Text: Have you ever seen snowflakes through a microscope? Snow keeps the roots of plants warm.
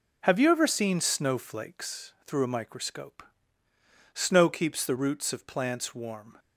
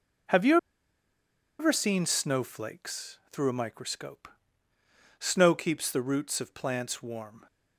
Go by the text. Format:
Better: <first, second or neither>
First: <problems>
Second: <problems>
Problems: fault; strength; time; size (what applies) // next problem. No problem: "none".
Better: first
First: none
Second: pauses between "you" and "ever"; at 0.5 s; 1.0 s long